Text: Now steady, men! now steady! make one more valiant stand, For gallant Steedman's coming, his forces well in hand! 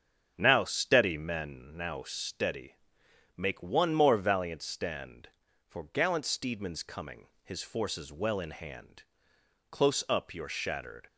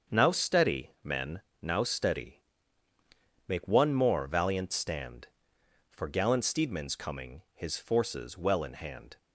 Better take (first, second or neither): second